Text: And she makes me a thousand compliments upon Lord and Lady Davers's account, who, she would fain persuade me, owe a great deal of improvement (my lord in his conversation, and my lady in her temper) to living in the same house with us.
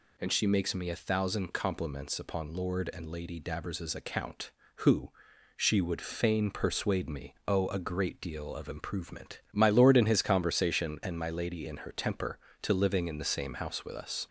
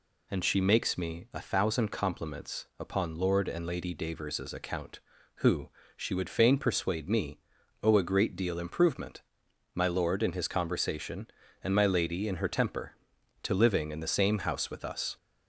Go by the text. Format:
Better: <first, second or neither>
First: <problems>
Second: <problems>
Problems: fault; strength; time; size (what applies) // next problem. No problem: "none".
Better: first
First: none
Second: skips "of"; at 8.5 s